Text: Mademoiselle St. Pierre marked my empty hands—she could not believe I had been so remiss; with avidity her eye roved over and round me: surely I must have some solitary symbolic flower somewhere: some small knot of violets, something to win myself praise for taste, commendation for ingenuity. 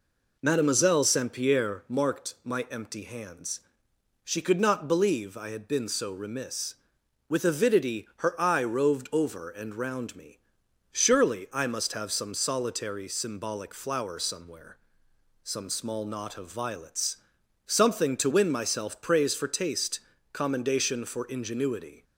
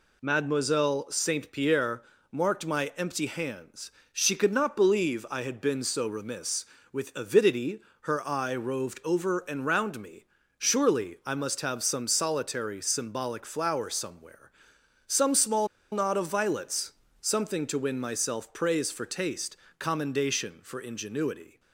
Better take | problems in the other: first | pauses between "Pierre" and "marked"; slight; at 2.0 s; 0.30 s long // pauses between "avidity" and "her"; slight; at 7.8 s; 0.18 s long // pauses between "small" and "knot"; slight; at 15.6 s; 0.24 s long

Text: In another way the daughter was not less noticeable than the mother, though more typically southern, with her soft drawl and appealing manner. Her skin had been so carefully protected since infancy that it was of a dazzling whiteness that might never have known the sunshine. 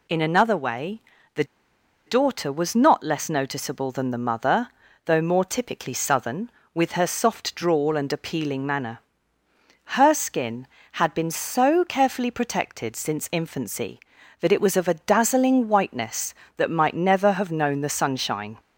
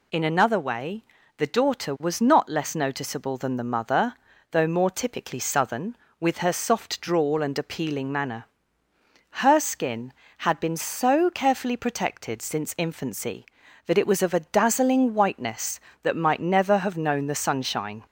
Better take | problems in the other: second | pauses between "way" and "the"; slight; at 1.0 s; 0.34 s long; slight in the second // pauses between "the" and "daughter"; noticeable; at 1.4 s; 0.63 s long

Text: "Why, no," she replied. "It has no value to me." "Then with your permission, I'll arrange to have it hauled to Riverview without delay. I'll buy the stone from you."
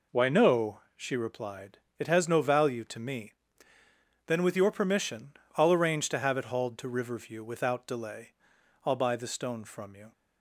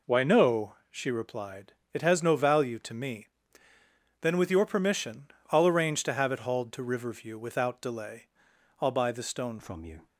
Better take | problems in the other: first | changes voice at "from"; from 9.5 s on; 0.5 s long

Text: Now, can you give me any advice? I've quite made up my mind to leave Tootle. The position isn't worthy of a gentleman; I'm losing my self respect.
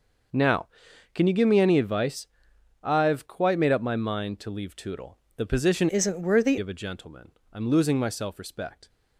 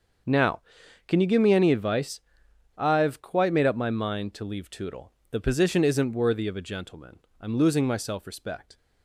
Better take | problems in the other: second | starts louder than the rest; noticeable; until 1.8 s; 6 dB; also in the second // changes voice from "isn't" to "worthy"; from 5.8 to 6.5 s; 0.7 s long

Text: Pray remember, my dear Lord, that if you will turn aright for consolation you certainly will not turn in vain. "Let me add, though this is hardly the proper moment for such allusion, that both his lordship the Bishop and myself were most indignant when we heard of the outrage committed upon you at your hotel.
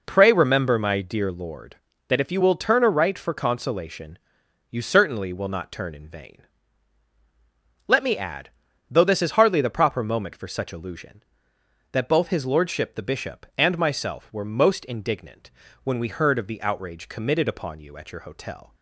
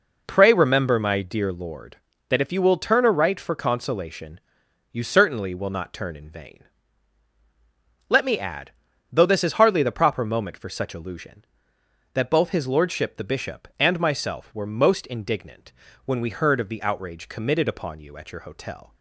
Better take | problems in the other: neither | pauses between "consolation" and "you"; noticeable; the same in both // pauses between "indignant" and "when"; slight; the same in both

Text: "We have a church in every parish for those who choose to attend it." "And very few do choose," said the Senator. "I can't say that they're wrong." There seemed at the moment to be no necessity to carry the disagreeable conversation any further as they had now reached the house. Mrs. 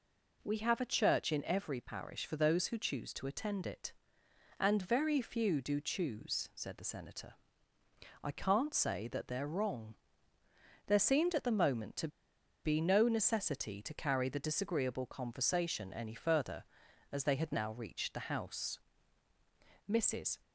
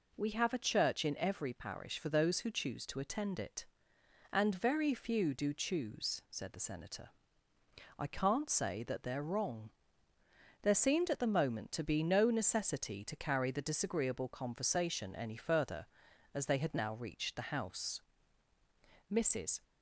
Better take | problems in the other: second | pauses between "to" and "be"; noticeable; at 12.0 s; 0.56 s long

